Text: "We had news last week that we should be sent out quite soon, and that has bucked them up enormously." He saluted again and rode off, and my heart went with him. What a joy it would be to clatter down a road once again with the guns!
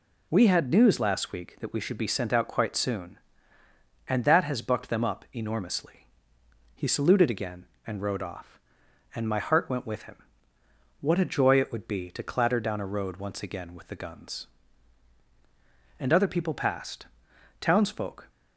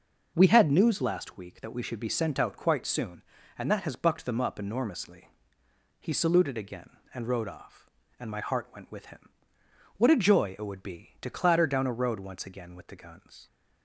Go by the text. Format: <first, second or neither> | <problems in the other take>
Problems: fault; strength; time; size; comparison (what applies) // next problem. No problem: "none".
second | goes on to say "And other people passed Townsfolk"; strong; from 15.9 s on; 2.2 s long